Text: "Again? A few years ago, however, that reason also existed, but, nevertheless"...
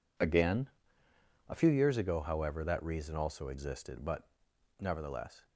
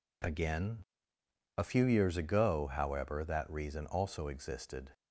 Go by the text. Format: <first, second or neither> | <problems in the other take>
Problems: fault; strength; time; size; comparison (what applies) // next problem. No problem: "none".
first | stops before "but nevertheless"; at 4.9 s